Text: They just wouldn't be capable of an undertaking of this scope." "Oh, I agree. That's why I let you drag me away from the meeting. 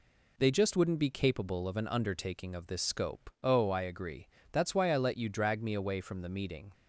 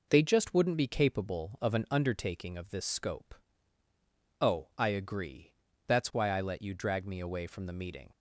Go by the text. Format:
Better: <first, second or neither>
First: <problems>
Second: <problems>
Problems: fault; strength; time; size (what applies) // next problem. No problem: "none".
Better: neither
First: none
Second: none